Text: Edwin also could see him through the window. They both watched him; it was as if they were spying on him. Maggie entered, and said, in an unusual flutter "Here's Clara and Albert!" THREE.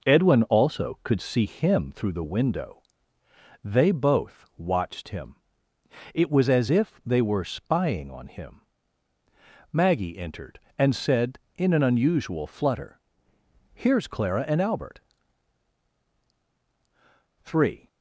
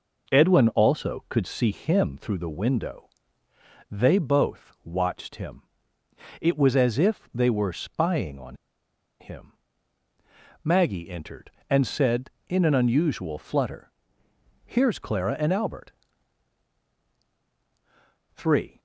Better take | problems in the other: first | pauses between "on" and "him"; noticeable; at 8.5 s; 0.64 s long // pauses between "flutter" and "Here's"; noticeable; at 13.8 s; 0.76 s long; noticeable in the first

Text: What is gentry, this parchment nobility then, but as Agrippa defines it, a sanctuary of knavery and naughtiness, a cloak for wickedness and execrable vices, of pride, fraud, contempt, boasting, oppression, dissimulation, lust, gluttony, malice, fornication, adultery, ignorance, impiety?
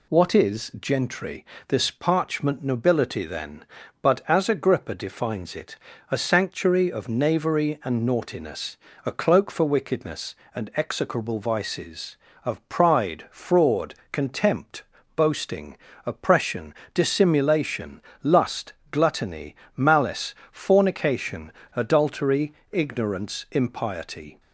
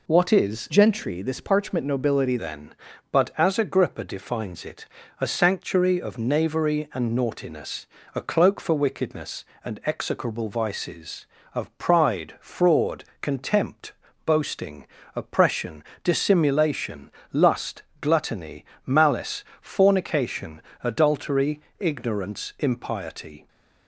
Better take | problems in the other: first | changes voice from "gentry" to "nobility"; from 0.6 to 2.3 s; 1.7 s long

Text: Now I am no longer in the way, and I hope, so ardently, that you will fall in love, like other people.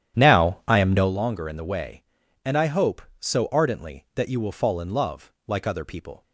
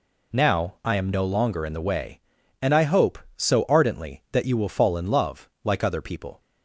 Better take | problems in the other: second | starts louder than the rest; strong; until 1.1 s; 10.5 dB

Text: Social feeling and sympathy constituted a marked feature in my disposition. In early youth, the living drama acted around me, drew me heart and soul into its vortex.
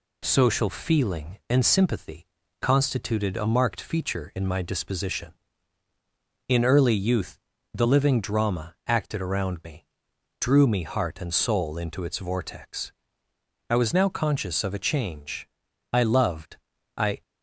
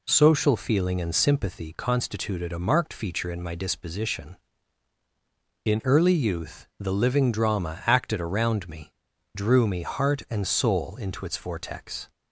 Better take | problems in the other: second | pauses between "sympathy" and "constituted"; slight; at 2.2 s; 0.36 s long // goes on to say "I was now conscious of a change I loved I"; strong; from 13.6 s on; 3.5 s long

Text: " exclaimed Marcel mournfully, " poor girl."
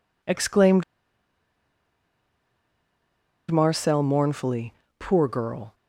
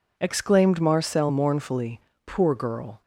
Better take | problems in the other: second | pauses between "exclaimed" and "Marcel"; strong; at 0.8 s; 2.6 s long

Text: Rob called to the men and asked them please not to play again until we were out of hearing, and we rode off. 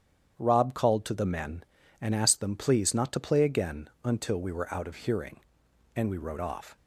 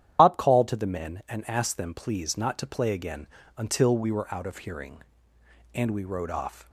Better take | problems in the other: first | loses the start of "Rob"; at 0.1 s; 100 ms // starts louder than the rest; strong; until 1.2 s; 10 dB; strong in the first // pauses between "again" and "until"; slight; at 3.2 s; 0.30 s long; slight in the first

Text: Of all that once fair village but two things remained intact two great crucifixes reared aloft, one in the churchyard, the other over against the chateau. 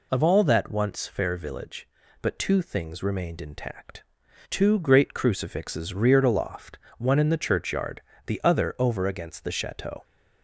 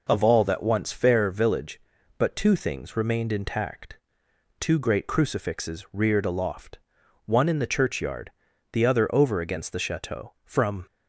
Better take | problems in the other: first | pauses between "intact" and "two"; noticeable; at 3.9 s; 0.60 s long; noticeable in the first // goes on to say "From"; slight; from 10.4 s on; 0.40 s long

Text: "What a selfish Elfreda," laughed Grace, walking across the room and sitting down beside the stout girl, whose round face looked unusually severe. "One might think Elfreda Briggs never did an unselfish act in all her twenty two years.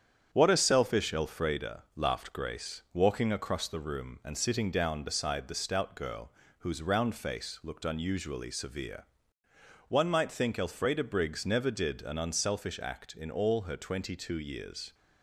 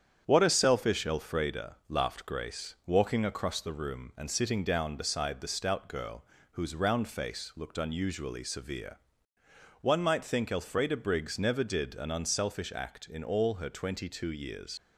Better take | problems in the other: first | starts louder than the rest; strong; until 1.2 s; 8.5 dB; strong in the first // leaves "years" unfinished; at 14.7 s; 95 ms

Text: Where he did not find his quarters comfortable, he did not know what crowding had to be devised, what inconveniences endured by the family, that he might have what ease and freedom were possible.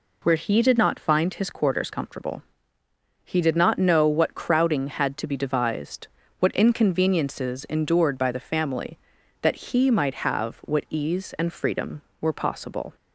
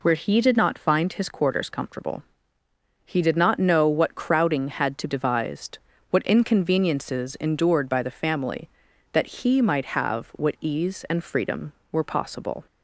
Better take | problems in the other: first | skips "be"; at 5.0 s

